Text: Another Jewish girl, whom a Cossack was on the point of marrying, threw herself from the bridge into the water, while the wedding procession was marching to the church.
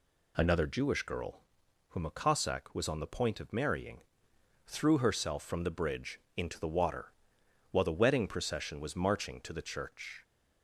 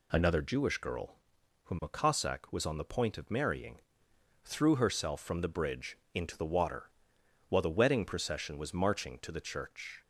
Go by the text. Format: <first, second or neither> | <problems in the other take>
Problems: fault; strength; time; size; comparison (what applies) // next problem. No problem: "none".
neither | pauses between "bridge" and "into"; slight; the same in both